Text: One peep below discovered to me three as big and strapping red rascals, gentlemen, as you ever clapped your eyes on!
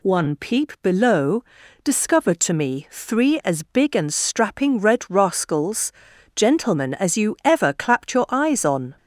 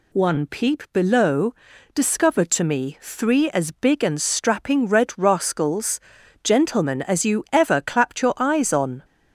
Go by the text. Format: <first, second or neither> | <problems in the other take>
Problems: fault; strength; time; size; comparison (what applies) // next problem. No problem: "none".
neither | pauses between "below" and "discovered"; the same in both